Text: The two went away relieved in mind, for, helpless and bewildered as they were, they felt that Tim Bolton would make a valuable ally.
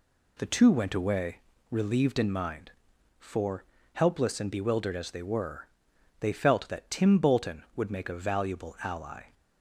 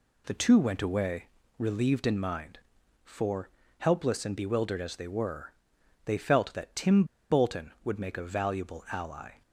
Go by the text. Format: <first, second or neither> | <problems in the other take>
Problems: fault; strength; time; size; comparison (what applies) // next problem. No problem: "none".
first | pauses between "away" and "relieved"; slight; at 1.2 s; 0.32 s long; slight in the first // pauses between "Tim" and "Bolton"; slight; at 7.0 s; 0.25 s long